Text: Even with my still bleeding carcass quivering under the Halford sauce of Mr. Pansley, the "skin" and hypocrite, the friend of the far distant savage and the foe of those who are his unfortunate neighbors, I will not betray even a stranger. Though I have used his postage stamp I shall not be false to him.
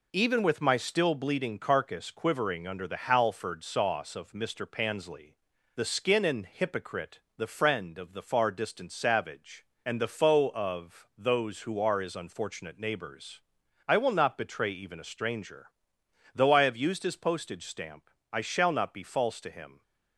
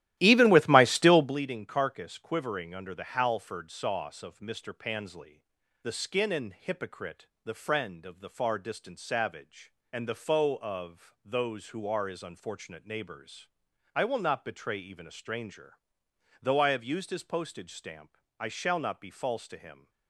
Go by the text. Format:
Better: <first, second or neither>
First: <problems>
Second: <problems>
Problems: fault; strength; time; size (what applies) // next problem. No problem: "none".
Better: first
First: pauses between "stamp" and "I"; slight; at 18.0 s; 0.24 s long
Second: starts louder than the rest; strong; until 1.4 s; 14 dB // pauses between "stamp" and "I"; slight; at 18.1 s; 0.24 s long